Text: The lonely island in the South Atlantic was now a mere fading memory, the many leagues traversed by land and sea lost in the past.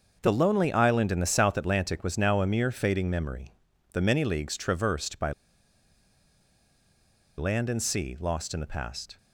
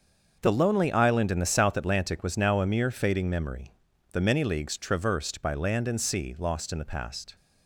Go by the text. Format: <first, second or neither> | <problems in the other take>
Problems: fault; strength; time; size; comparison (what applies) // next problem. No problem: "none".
second | starts louder than the rest; until 1.2 s; 6.5 dB; also in the second // pauses between "by" and "land"; strong; at 5.3 s; 2.0 s long